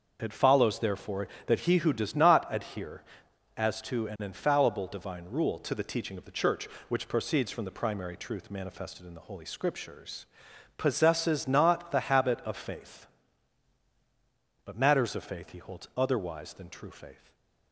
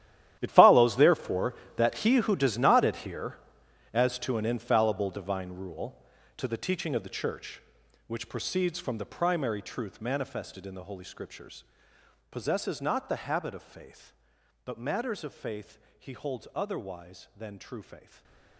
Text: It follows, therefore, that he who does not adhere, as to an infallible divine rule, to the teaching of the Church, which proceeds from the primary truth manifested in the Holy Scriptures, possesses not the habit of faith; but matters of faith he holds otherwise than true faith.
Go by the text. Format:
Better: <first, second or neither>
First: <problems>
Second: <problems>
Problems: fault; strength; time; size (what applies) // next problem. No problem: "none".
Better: first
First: starts louder than the rest; until 1.2 s; 6.5 dB // stays silent after the last word; slight; from 17.1 s on; 0.6 s long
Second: gets quieter; strong; throughout; 16 dB // starts louder than the rest; strong; until 1.4 s; 12 dB // pauses between "faith" and "he"; slight; at 15.7 s; 0.18 s long // stays silent after the last word; slight; from 17.9 s on; 0.6 s long